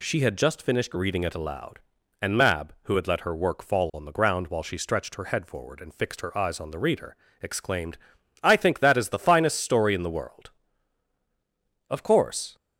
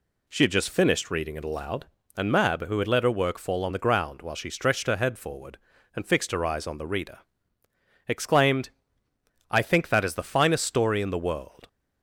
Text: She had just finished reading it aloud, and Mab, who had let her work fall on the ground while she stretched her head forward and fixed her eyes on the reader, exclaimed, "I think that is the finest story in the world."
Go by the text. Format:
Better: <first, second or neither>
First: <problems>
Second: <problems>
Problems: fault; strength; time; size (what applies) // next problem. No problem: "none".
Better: second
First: goes on to say "Of course"; noticeable; from 11.8 s on; 0.66 s long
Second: none